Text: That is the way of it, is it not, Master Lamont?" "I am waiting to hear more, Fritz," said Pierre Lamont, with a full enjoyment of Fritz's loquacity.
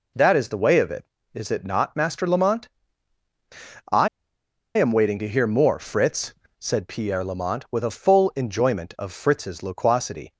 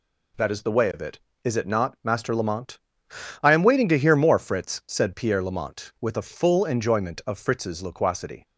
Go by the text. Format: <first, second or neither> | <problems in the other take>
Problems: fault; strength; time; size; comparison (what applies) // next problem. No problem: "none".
second | pauses between "I" and "am"; noticeable; at 4.0 s; 0.69 s long